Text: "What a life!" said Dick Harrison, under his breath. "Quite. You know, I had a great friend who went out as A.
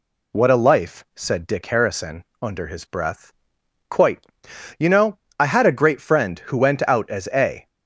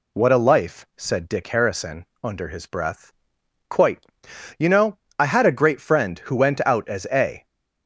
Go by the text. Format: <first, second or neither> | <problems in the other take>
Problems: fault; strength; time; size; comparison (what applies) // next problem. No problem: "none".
neither | none